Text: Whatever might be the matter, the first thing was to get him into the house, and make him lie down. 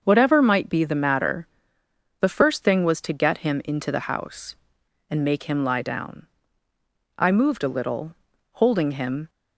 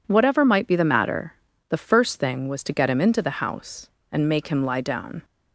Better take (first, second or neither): second